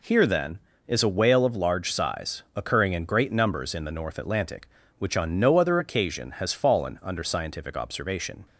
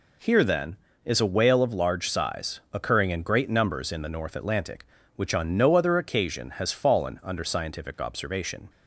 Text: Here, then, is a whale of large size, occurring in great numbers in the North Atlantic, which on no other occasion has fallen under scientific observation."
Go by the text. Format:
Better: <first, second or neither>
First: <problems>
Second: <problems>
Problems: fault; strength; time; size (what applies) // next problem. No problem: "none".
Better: neither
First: none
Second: none